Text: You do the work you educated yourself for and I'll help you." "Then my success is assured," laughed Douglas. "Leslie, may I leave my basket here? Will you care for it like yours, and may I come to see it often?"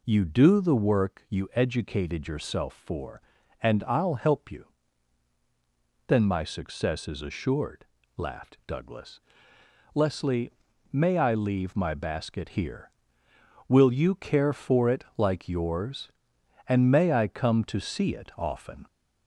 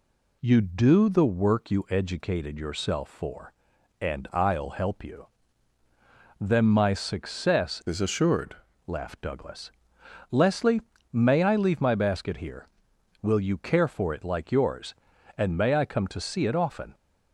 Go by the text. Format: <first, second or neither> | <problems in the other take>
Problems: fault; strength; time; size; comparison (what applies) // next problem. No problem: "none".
first | changes voice from "is" to "assured"; from 7.8 to 8.5 s; 0.7 s long